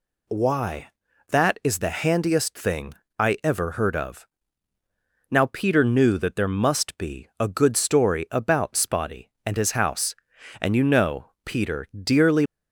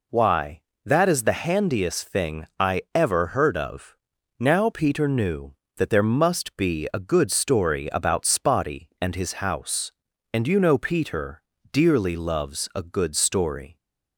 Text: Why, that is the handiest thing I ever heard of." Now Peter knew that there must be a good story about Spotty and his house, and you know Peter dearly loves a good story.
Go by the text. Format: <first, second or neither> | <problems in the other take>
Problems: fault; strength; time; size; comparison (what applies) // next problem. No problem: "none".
second | pauses between "thing" and "I"; slight; at 2.9 s; 0.26 s long // pauses between "know" and "Peter"; slight; at 11.3 s; 0.16 s long // pauses between "Peter" and "dearly"; slight; at 11.8 s; 0.18 s long; slight in the second // stops before "loves a good story"; at 12.4 s